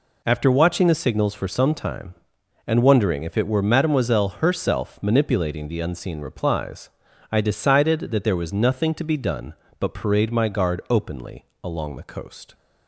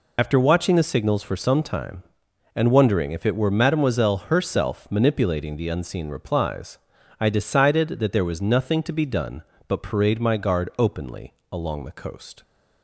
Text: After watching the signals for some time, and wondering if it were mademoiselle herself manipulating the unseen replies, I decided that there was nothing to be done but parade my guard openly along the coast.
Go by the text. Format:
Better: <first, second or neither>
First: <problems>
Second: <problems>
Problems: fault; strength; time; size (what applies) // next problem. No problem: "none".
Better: first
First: pauses between "openly" and "along"; slight; at 11.4 s; 0.20 s long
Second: loses the start of "After"; at 0.1 s; 60 ms // pauses between "openly" and "along"; slight; at 11.3 s; 0.20 s long